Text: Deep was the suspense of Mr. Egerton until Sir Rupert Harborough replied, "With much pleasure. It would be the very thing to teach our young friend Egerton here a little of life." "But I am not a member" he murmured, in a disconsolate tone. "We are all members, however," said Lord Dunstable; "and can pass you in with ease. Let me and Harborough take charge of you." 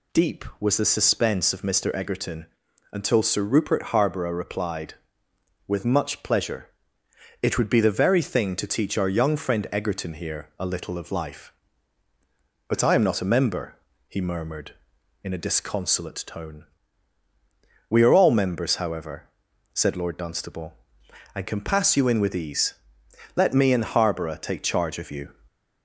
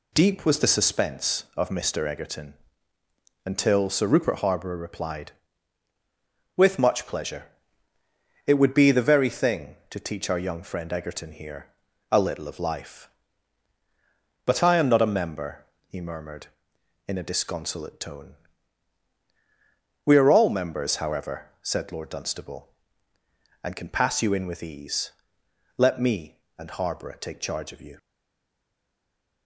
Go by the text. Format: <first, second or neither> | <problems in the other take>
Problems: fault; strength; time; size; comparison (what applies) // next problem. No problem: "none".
first | pauses between "Egerton" and "until"; noticeable; at 2.5 s; 0.90 s long; also in the first // pauses between "here" and "a"; at 11.7 s; 0.38 s long // pauses between "member" and "he"; slight; at 15.6 s; 0.22 s long; slight in the first // stays silent after the last word; noticeable; from 27.9 s on; 1.5 s long